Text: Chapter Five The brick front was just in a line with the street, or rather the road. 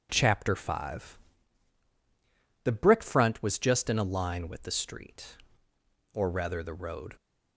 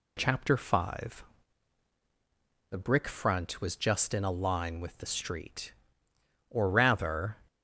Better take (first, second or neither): first